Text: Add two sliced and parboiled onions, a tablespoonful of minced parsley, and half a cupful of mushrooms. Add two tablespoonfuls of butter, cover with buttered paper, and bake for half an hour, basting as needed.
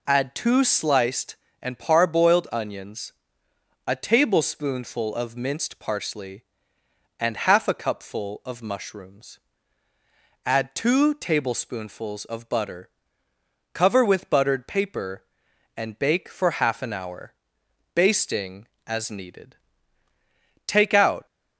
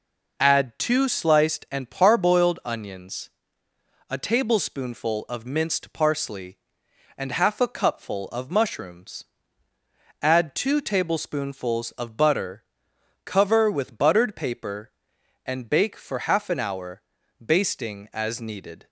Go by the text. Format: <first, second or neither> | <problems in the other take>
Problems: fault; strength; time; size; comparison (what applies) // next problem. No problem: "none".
second | goes on to say "Take out"; from 20.6 s on; 0.58 s long